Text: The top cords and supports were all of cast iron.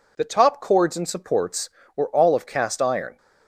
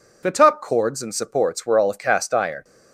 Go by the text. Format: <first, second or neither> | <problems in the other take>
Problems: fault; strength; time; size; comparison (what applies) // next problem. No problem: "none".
neither | none